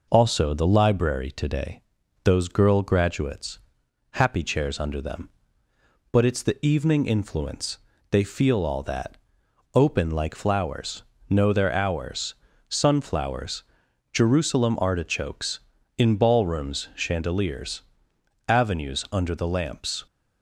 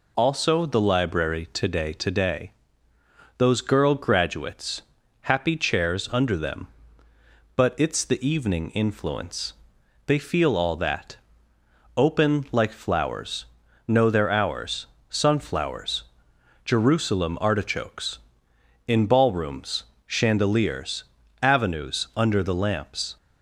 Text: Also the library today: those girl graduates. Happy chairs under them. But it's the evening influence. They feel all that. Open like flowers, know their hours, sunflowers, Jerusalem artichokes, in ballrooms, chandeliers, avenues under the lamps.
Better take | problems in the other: first | says "today" twice; at 1.9 s

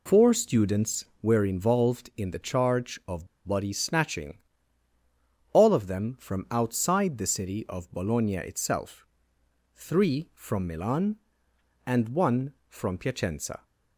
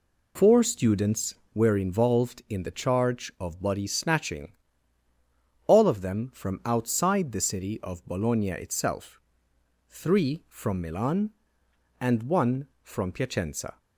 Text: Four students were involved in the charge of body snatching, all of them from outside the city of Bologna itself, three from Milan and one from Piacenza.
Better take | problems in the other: second | pauses between "of" and "body"; slight; at 3.2 s; 0.19 s long

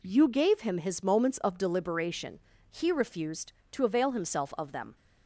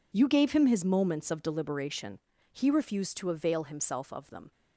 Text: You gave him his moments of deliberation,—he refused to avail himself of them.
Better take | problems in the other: neither | none

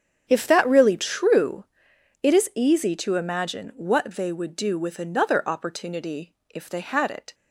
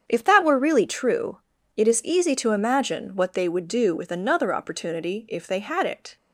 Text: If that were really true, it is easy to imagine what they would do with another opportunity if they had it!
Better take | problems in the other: second | starts louder than the rest; strong; until 1.2 s; 8 dB; strong in the second // skips "were"; at 0.6 s // pauses between "opportunity" and "if"; slight; at 6.3 s; 0.20 s long

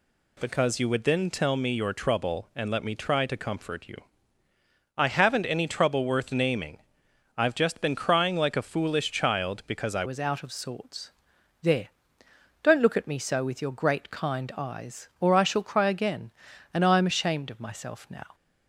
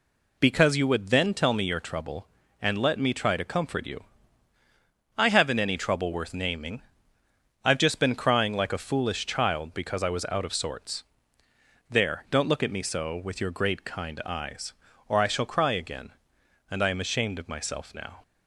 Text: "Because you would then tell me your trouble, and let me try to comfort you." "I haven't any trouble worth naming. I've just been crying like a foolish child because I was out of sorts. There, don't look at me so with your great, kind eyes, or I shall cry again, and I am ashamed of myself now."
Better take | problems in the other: second | changes voice at "was"; from 10.0 s on; 8.3 s long

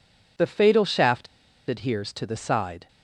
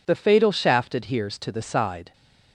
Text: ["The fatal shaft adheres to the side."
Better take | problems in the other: second | pauses between "shaft" and "adheres"; at 1.2 s; 0.43 s long

